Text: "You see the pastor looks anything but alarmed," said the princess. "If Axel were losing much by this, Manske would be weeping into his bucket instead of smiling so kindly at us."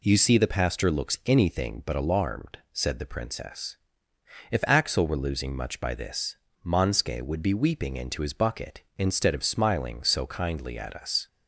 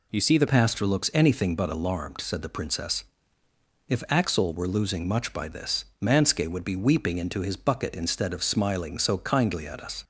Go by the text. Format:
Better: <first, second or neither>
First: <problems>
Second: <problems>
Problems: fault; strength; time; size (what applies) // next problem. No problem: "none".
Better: first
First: none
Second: changes voice at "pastor"; from 0.4 s on; 9.6 s long